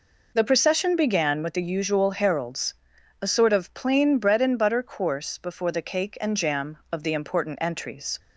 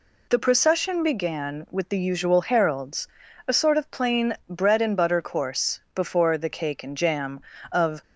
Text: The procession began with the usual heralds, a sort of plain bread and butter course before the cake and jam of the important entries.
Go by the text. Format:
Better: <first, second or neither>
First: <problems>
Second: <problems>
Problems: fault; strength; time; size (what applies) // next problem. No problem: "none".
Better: first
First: none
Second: stops before "the important entries"; at 8.0 s